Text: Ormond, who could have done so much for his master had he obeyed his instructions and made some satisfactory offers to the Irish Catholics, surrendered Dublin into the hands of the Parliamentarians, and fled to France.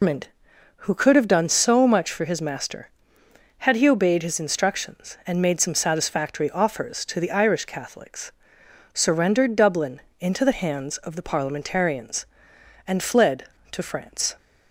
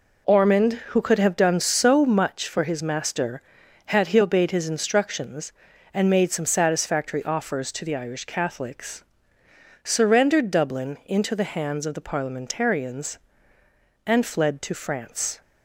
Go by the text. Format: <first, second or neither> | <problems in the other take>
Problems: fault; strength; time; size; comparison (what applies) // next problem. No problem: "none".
second | loses the start of "Ormond"; at 0.0 s; 155 ms // pauses between "Dublin" and "into"; slight; at 10.0 s; 0.20 s long